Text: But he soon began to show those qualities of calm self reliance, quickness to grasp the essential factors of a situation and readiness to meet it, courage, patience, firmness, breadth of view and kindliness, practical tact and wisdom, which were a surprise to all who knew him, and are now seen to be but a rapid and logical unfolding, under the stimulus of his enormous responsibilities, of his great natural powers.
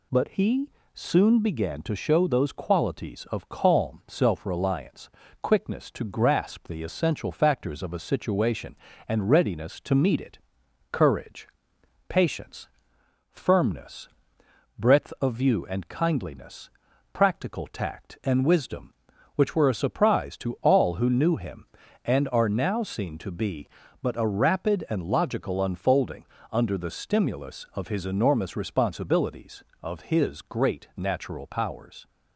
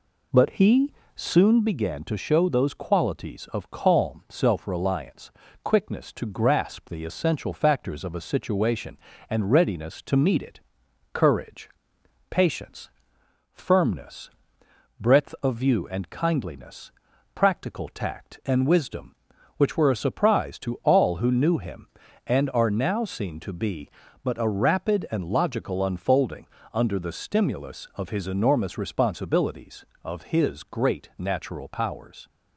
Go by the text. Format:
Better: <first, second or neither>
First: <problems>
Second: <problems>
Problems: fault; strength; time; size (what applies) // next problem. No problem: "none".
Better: first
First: pauses between "he" and "soon"; slight; at 0.6 s; 0.24 s long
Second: starts louder than the rest; slight; until 1.4 s; 3 dB // pauses between "he" and "soon"; slight; at 0.9 s; 0.24 s long